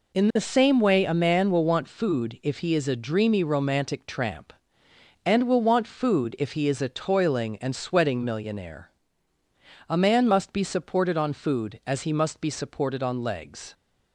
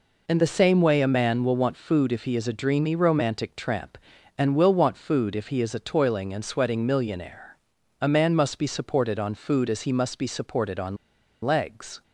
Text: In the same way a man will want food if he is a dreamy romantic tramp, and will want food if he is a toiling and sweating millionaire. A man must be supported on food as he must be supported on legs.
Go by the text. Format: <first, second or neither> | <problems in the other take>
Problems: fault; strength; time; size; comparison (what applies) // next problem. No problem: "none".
first | pauses between "on" and "legs"; noticeable; at 10.9 s; 0.47 s long